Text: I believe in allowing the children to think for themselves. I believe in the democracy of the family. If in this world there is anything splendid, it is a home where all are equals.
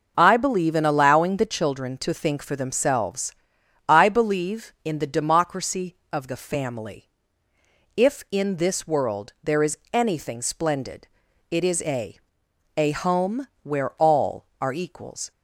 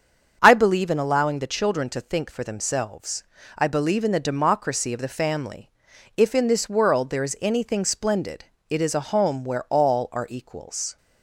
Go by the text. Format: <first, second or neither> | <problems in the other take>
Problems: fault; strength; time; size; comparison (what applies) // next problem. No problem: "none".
second | starts louder than the rest; noticeable; until 1.1 s; 6 dB; strong in the second // pauses between "is" and "anything"; slight; at 9.7 s; 0.16 s long // says "a" twice; at 12.7 s // pauses between "home" and "where"; slight; at 13.4 s; 0.16 s long